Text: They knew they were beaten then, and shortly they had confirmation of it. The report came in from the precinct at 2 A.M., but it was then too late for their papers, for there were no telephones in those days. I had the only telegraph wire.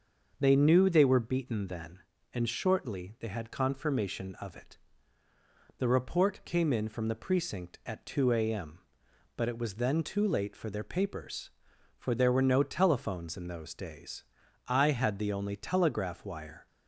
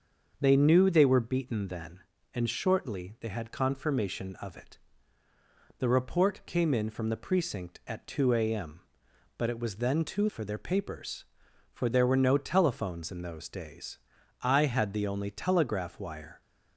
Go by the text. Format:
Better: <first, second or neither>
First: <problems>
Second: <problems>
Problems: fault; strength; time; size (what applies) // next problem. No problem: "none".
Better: first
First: starts louder than the rest; until 1.3 s; 6.5 dB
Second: starts louder than the rest; until 1.4 s; 6.5 dB // skips "late"; at 10.2 s